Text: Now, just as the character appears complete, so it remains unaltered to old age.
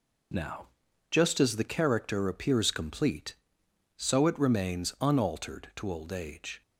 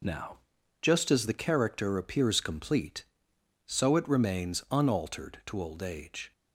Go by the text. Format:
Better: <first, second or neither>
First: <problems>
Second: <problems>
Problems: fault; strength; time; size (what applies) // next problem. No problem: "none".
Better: neither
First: none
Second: none